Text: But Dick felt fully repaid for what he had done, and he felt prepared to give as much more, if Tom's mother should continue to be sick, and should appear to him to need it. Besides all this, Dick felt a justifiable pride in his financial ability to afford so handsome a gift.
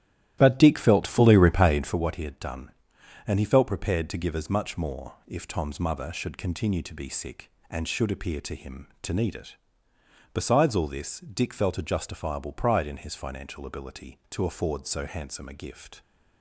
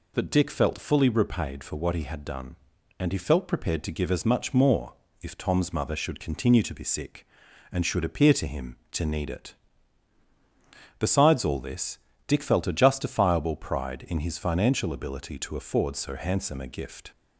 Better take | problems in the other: second | starts louder than the rest; strong; until 2.0 s; 13 dB

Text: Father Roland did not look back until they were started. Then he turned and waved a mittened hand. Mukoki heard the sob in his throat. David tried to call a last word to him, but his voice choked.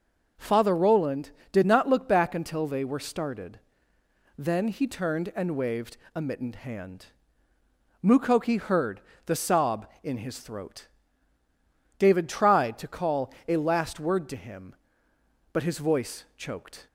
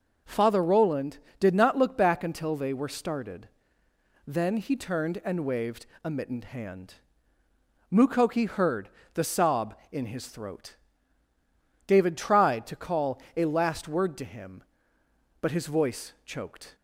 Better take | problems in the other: neither | pauses between "waved" and "a"; slight; the same in both // pauses between "heard" and "the"; slight; the same in both

